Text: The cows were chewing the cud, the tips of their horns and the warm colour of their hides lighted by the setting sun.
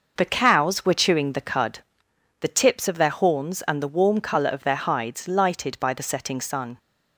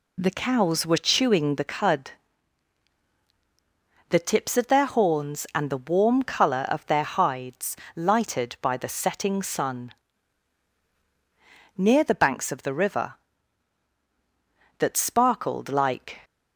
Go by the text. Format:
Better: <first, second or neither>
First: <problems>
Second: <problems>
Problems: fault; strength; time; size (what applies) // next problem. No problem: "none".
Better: first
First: none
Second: pauses between "hides" and "lighted"; slight; at 7.7 s; 0.18 s long // goes on to say "Near the banks of the river that sparkled like"; strong; from 11.7 s on; 4.4 s long